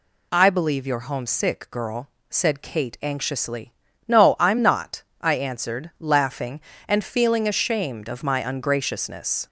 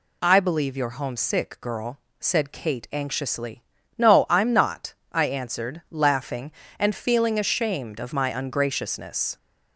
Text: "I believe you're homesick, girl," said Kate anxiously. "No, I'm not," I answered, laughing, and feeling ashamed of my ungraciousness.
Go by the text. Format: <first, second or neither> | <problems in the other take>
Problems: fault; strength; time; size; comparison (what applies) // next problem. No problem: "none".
neither | none